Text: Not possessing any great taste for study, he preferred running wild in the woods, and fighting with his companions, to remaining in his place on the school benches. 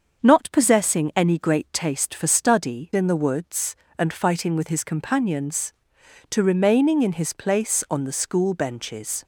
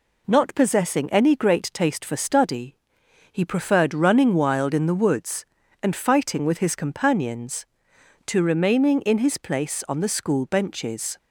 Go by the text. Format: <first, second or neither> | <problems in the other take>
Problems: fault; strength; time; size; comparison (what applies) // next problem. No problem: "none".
second | starts louder than the rest; until 1.2 s; 6.5 dB // skips "he preferred running wild"; at 2.9 s